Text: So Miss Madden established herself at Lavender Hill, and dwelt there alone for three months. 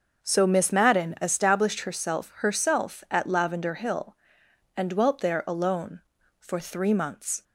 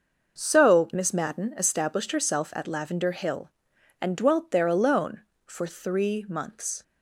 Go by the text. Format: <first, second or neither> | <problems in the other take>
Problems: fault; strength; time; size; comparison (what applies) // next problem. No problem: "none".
second | starts louder than the rest; until 1.2 s; 6.5 dB // says "herself" twice; at 2.3 s